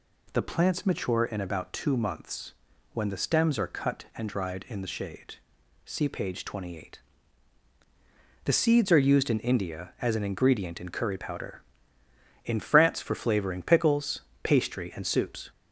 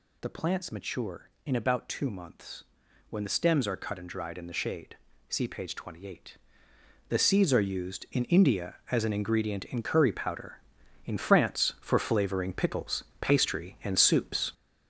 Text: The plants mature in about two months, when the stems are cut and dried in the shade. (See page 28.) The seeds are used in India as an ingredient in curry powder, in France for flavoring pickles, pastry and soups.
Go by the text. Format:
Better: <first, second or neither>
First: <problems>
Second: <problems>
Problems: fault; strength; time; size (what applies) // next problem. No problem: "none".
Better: first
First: none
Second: gets louder; strong; throughout; 7 dB